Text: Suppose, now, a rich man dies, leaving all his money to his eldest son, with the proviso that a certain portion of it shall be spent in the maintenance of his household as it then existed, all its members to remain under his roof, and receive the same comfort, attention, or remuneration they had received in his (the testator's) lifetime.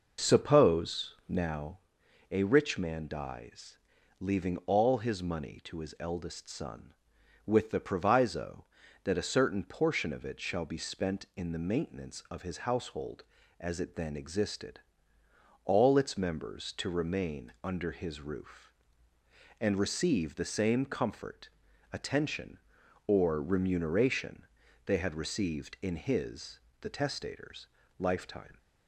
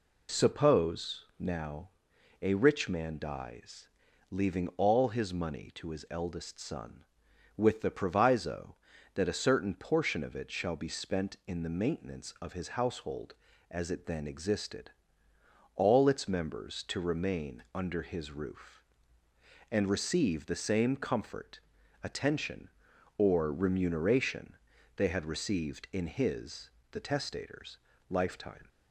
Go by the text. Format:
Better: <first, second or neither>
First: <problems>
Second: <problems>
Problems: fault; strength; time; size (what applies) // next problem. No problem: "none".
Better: second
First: starts louder than the rest; noticeable; until 1.8 s; 5.5 dB // pauses between "remuneration" and "they"; at 24.4 s; 0.40 s long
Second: pauses between "remuneration" and "they"; at 24.5 s; 0.40 s long